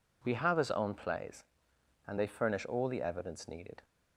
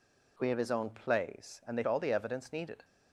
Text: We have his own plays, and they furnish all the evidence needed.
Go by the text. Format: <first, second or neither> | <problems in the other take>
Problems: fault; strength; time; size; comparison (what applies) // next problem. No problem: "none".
first | skips "furnish"; at 1.8 s